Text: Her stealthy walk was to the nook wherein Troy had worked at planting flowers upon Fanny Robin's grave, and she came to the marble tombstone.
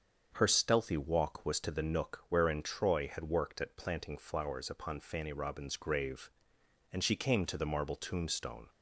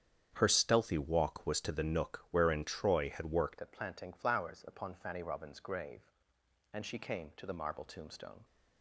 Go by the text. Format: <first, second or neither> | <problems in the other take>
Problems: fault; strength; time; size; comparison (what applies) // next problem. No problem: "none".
first | starts louder than the rest; strong; until 1.3 s; 9 dB; also in the first // changes voice at "at"; from 3.6 s on; 4.8 s long